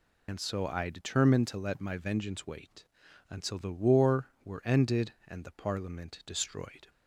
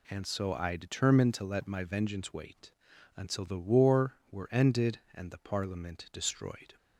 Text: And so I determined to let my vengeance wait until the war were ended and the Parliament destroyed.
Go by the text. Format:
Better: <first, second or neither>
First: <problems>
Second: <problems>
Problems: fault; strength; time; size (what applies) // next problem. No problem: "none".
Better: second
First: loses the start of "And"; at 0.2 s; 90 ms // pauses between "wait" and "until"; at 2.8 s; 0.44 s long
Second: pauses between "wait" and "until"; at 2.7 s; 0.44 s long